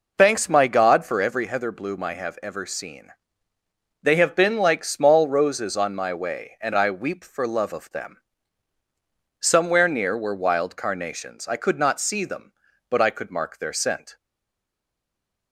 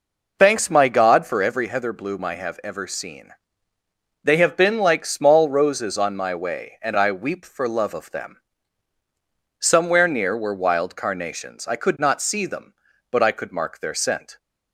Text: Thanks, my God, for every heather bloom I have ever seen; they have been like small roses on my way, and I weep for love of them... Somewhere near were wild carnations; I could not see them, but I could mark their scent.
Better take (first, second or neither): second